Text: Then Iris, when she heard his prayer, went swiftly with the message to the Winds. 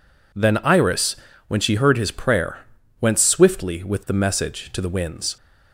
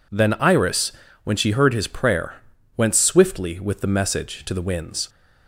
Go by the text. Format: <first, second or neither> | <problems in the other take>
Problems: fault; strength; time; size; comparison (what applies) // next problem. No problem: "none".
neither | none